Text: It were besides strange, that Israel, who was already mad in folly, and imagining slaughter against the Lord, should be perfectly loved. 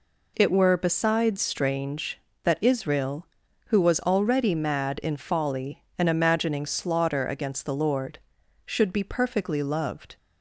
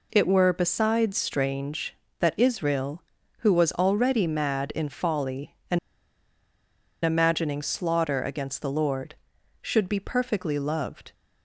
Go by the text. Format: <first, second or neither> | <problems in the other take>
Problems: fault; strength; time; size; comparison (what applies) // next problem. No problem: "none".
first | pauses between "and" and "imagining"; strong; at 5.7 s; 1.2 s long